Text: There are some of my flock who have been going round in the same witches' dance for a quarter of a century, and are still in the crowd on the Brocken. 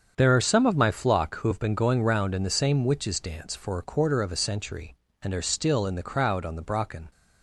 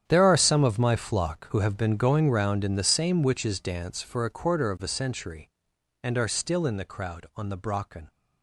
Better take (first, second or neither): first